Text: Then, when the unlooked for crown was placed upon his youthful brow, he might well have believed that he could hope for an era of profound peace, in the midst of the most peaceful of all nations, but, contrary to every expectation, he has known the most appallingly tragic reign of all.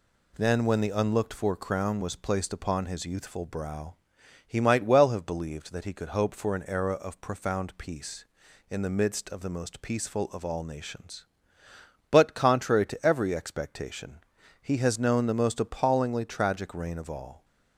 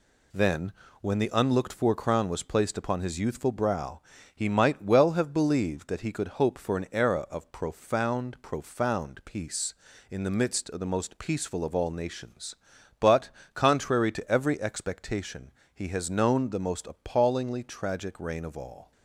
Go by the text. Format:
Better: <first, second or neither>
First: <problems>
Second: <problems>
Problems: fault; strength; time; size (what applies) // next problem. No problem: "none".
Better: first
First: none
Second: says "profound" twice; at 8.4 s